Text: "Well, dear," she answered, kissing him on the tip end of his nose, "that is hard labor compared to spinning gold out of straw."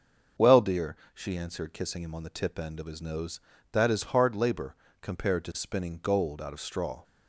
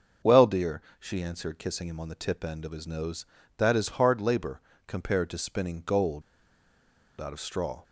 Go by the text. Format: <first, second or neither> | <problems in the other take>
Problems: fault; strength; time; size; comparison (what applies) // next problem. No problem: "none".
first | starts louder than the rest; until 1.4 s; 6 dB; also in the first // pauses between "labor" and "compared"; slight; at 4.6 s; 0.26 s long; slight in the first // pauses between "gold" and "out"; at 6.2 s; 0.99 s long